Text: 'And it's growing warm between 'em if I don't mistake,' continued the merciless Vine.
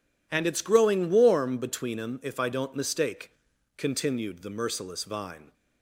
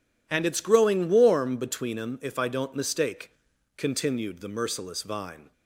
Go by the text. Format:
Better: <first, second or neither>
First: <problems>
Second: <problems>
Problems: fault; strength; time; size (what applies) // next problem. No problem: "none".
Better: neither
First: none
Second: none